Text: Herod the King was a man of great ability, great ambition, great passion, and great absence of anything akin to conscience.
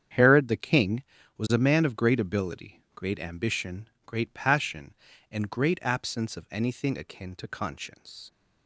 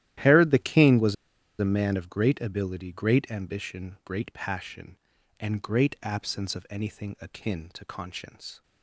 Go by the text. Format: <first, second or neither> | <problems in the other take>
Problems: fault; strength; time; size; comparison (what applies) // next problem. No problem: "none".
first | starts louder than the rest; strong; until 1.6 s; 13 dB; strong in the first // pauses between "was" and "a"; at 1.1 s; 0.44 s long